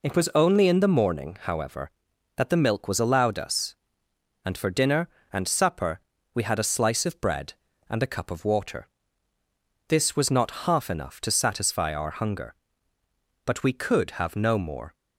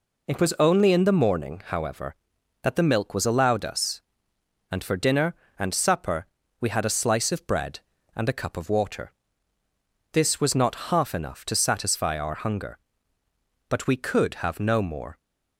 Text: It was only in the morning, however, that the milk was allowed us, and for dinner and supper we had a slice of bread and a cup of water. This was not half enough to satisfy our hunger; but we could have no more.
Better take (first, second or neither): neither